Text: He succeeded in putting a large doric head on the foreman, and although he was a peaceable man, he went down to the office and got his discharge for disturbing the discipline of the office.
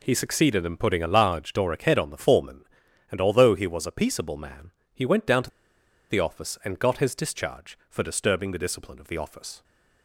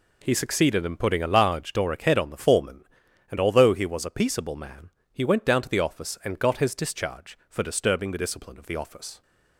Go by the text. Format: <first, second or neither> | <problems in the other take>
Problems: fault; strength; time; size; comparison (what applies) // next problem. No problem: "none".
second | pauses between "to" and "the"; noticeable; at 5.5 s; 0.59 s long